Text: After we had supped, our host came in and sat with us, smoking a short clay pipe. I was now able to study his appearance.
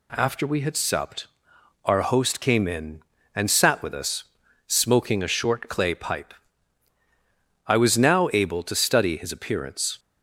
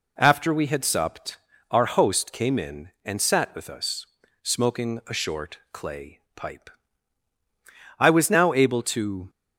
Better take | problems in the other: first | pauses between "short" and "clay"; slight; at 5.5 s; 0.16 s long // pauses between "clay" and "pipe"; slight; at 6.1 s; 0.16 s long // stops before "study his appearance"; at 9.2 s

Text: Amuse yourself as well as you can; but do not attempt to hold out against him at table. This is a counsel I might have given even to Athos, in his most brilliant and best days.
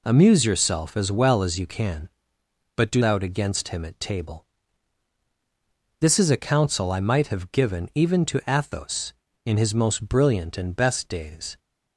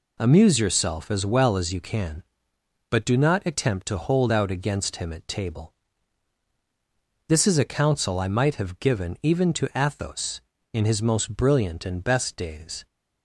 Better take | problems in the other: second | skips "not attempt to hold"; at 3.0 s

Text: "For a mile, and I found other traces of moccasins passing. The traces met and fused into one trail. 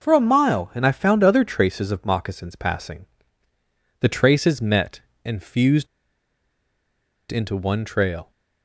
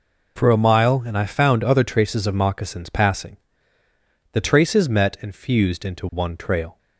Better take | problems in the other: second | pauses between "fused" and "into"; strong; at 5.8 s; 1.4 s long

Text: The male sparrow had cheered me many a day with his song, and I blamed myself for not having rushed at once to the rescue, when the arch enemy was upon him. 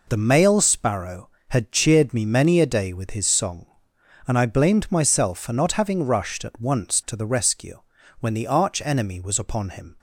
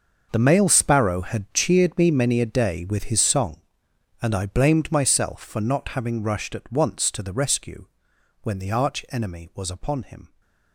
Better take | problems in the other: first | gets quieter; strong; throughout; 15.5 dB

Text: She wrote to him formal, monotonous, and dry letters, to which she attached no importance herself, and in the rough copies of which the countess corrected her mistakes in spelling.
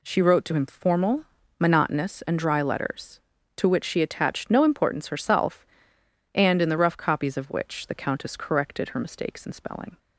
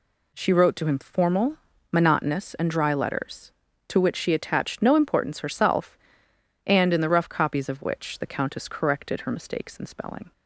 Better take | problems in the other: neither | none

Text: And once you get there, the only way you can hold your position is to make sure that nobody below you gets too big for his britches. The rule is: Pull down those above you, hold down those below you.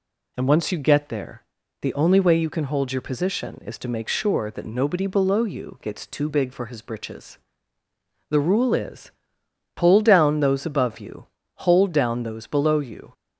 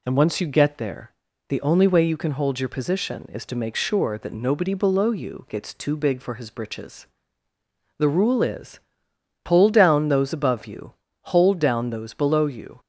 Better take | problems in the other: neither | none

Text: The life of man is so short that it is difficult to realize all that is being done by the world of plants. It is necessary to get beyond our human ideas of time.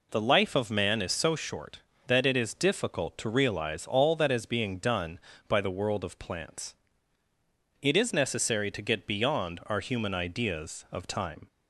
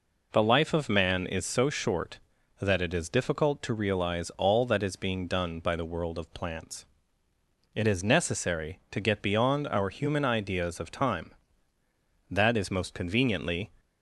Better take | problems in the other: first | goes on to say "That is most conveniently"; from 12.3 s on; 1.4 s long

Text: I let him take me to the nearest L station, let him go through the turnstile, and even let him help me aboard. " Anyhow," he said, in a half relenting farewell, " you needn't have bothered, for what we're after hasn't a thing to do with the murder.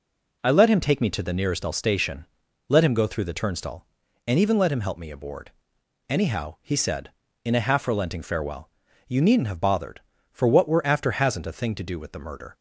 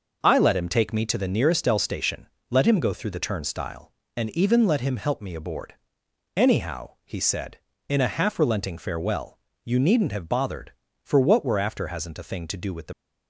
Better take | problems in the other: first | stops before "murder"; at 12.9 s

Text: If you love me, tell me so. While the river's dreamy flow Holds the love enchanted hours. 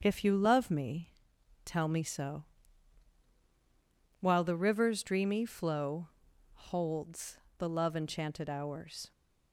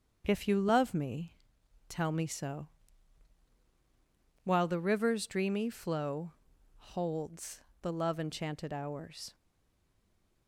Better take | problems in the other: first | starts louder than the rest; until 1.2 s; 7 dB; also in the first // pauses between "flow" and "Holds"; noticeable; at 6.3 s; 0.63 s long; noticeable in the first // pauses between "Holds" and "the"; slight; at 7.6 s; 0.20 s long; slight in the first // stays silent after the last word; from 9.3 s on; 1.1 s long

